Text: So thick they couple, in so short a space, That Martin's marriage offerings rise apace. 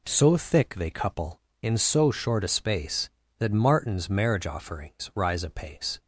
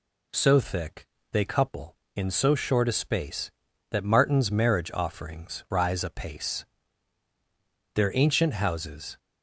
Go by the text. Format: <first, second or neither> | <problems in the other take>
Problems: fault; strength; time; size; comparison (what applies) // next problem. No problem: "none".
first | pauses between "thick" and "they"; slight; at 1.0 s; 0.24 s long // goes on to say "Their ancient houses"; noticeable; from 7.9 s on; 1.2 s long